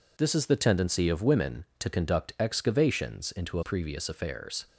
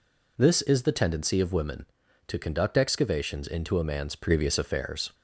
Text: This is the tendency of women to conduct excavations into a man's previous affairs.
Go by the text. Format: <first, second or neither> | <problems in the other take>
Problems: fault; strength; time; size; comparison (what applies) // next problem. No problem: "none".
second | skips "man's"; at 3.6 s